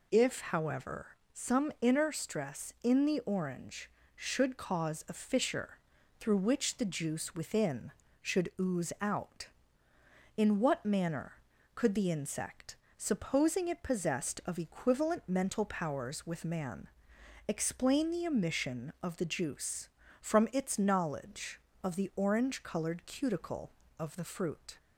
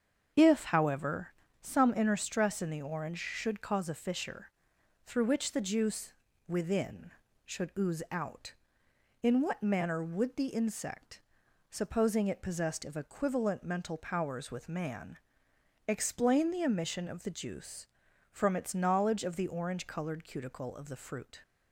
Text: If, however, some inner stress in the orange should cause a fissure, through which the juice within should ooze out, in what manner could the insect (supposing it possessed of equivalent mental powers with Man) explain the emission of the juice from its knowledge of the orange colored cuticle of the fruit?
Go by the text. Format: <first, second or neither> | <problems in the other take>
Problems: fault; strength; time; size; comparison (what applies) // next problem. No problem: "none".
first | starts louder than the rest; strong; until 1.6 s; 7 dB // pauses between "juice" and "within"; slight; at 6.1 s; 0.36 s long // says "would" for "could"; at 10.0 s